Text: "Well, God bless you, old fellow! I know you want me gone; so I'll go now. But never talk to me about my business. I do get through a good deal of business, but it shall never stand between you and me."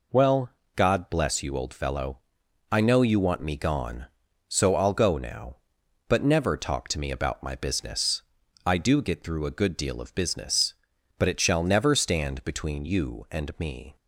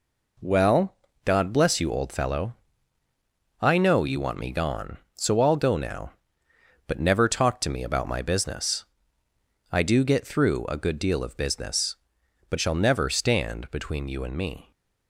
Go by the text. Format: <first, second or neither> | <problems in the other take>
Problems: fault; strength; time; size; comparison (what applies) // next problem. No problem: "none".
first | skips "it"; at 12.5 s